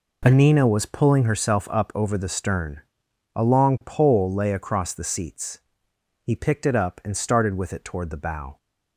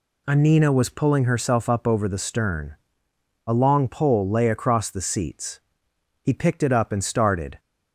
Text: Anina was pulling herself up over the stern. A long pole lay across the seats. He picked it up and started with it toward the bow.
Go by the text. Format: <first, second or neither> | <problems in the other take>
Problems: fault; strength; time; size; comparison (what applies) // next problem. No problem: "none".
first | stops before "with it toward the bow"; at 7.5 s